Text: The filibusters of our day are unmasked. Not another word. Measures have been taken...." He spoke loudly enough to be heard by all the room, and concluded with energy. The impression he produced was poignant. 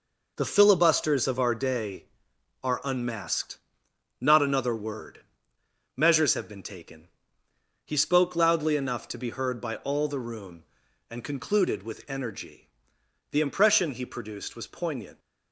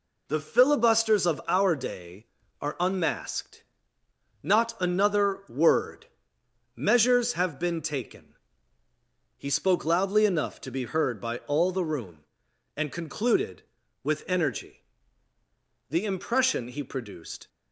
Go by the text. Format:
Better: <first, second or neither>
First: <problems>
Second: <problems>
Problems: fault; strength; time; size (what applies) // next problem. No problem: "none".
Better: first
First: none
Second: stops before "was poignant"; at 17.4 s